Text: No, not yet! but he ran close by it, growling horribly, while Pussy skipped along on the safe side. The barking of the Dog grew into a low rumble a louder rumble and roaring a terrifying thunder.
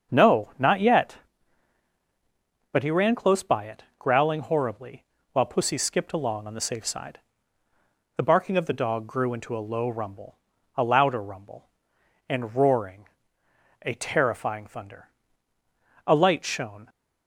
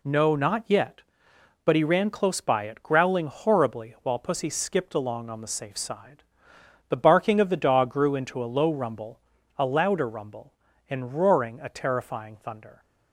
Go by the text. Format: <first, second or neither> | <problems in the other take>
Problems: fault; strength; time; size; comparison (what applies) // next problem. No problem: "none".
second | starts louder than the rest; until 1.1 s; 7 dB // pauses between "rumble" and "a"; at 10.3 s; 0.38 s long; also in the second // pauses between "roaring" and "a"; noticeable; at 13.0 s; 0.78 s long // goes on to say "A light shone"; noticeable; from 16.0 s on; 0.82 s long